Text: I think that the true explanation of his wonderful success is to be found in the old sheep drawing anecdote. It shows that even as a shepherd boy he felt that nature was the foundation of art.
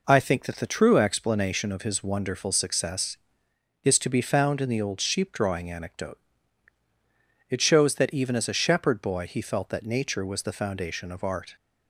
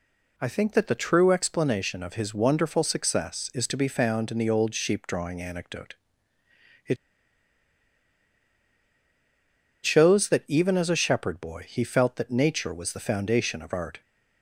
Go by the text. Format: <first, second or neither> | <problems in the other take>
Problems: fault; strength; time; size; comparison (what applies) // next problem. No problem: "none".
first | pauses between "It" and "shows"; strong; at 6.9 s; 2.8 s long